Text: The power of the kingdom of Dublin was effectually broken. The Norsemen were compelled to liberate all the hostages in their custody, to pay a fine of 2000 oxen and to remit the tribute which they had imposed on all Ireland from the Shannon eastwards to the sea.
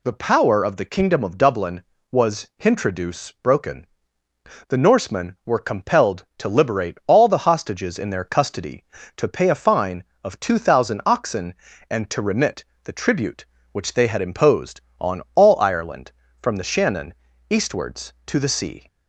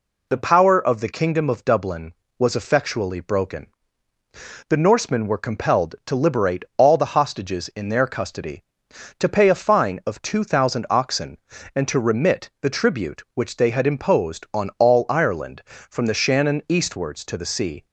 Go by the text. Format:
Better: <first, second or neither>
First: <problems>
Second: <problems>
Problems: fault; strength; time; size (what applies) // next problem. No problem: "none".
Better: second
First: says "hintroduce" for "effectually"; at 2.5 s // pauses between "remit" and "the"; slight; at 12.6 s; 0.22 s long // pauses between "Shannon" and "eastwards"; at 17.1 s; 0.38 s long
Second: none